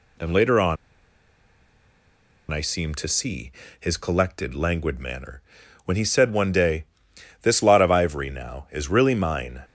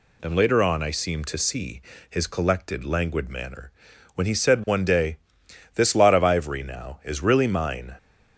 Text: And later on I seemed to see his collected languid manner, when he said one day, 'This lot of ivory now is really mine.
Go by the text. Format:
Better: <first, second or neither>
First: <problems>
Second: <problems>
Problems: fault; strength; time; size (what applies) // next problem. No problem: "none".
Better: second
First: pauses between "on" and "I"; strong; at 0.7 s; 1.7 s long // pauses between "see" and "his"; slight; at 3.5 s; 0.28 s long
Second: pauses between "see" and "his"; slight; at 1.8 s; 0.28 s long